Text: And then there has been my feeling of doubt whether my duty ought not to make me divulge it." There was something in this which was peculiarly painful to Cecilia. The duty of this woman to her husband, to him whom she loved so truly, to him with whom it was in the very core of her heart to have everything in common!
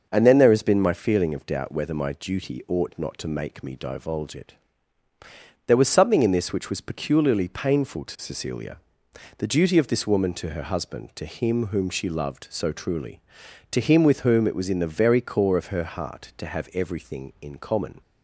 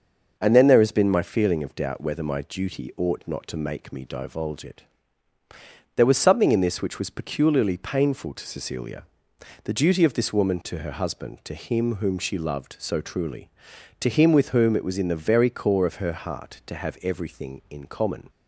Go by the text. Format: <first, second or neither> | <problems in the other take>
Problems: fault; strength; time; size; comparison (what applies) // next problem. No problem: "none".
neither | starts louder than the rest; noticeable; the same in both